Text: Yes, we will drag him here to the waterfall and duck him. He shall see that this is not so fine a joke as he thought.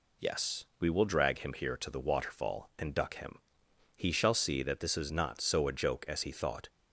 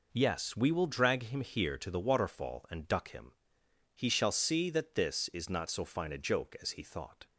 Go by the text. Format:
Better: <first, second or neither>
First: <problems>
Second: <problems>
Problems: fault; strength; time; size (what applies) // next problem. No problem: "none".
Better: second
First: skips "fine"; at 5.6 s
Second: none